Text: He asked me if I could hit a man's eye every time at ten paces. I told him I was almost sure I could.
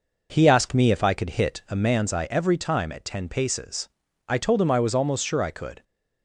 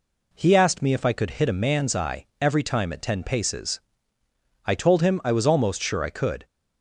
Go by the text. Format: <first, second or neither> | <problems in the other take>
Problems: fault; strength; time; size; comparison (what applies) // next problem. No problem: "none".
second | starts louder than the rest; noticeable; until 2.0 s; 5 dB